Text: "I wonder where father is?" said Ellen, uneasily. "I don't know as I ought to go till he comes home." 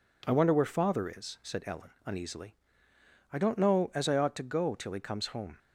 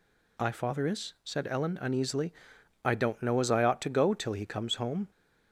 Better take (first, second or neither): first